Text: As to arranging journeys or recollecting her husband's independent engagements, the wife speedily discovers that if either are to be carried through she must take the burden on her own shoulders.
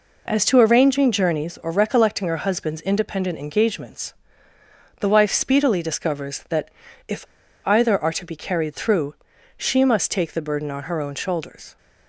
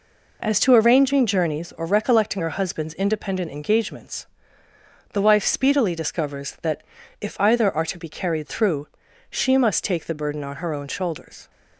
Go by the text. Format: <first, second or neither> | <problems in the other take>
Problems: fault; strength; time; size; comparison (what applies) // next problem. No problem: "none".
second | pauses between "that" and "if"; at 6.6 s; 0.38 s long; also in the second // pauses between "if" and "either"; at 7.2 s; 0.42 s long // pauses between "through" and "she"; at 9.1 s; 0.44 s long; also in the second